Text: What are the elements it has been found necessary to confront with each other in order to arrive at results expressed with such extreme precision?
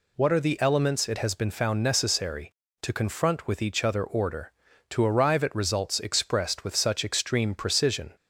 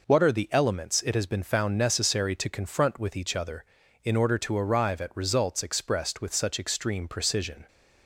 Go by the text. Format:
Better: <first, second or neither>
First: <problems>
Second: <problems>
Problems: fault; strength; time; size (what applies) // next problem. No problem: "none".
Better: second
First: skips "in"; at 4.0 s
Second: none